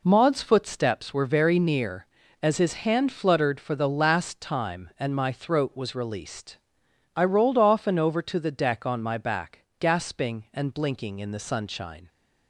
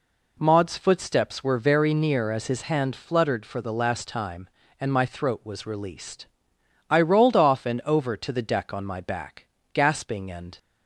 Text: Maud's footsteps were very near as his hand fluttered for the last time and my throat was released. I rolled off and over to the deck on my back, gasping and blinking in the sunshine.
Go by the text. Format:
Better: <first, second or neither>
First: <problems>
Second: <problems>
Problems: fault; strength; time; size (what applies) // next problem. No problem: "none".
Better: first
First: none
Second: stops before "blinking in the sunshine"; at 10.5 s